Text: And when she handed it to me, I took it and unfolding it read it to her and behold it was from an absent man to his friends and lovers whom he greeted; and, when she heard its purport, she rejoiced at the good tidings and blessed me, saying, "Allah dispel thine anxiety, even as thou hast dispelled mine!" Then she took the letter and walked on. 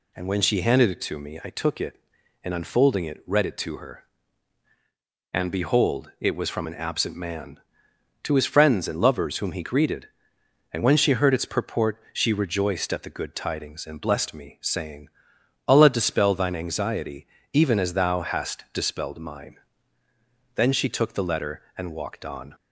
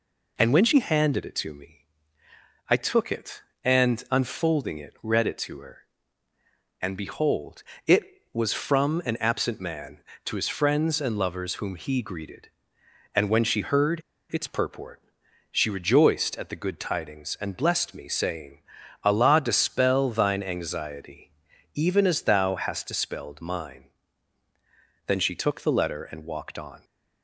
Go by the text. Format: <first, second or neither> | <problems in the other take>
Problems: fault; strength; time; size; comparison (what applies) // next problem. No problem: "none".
first | pauses between "behold" and "it"; slight; at 7.6 s; 0.24 s long // pauses between "heard" and "its"; slight; at 14.0 s; 0.29 s long